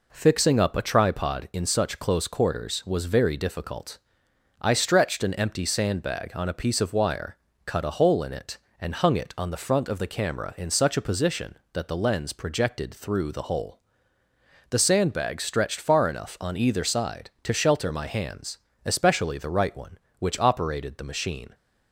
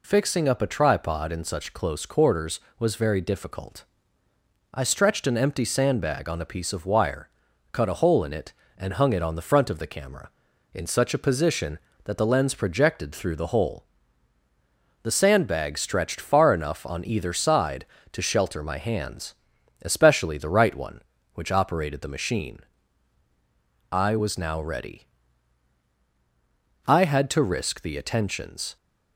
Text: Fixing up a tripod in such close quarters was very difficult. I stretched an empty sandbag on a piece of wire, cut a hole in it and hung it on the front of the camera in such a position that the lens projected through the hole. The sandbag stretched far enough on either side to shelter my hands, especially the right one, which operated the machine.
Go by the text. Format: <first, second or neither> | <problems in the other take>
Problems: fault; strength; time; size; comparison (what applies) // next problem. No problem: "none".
first | goes on to say "I was now ready I had to risk the attentions"; strong; from 23.9 s on; 4.8 s long